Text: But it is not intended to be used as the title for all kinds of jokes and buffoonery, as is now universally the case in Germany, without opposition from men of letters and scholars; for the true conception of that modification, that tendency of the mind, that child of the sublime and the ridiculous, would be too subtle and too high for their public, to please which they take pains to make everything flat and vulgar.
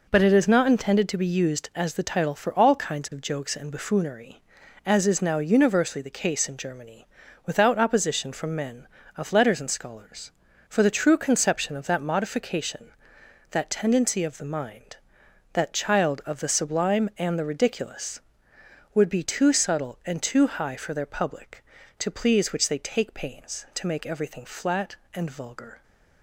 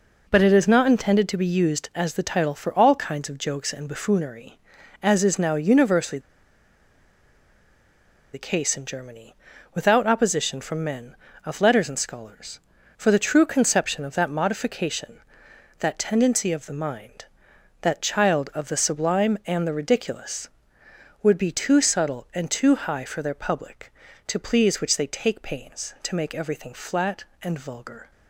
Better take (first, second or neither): first